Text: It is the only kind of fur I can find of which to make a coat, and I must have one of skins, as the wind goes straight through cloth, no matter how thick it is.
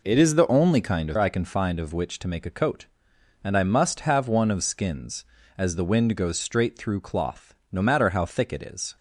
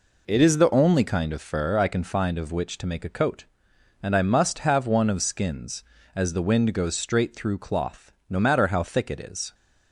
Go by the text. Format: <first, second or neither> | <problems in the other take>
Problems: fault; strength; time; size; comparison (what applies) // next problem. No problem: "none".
second | skips "fur"; at 1.1 s